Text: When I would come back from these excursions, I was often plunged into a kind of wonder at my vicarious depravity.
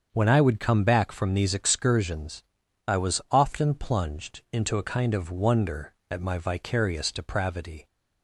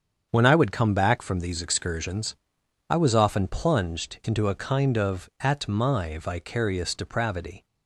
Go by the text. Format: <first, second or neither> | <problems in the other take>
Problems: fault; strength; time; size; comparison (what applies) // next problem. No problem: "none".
first | starts louder than the rest; strong; until 1.3 s; 7.5 dB; also in the first // skips "wonder"; at 5.3 s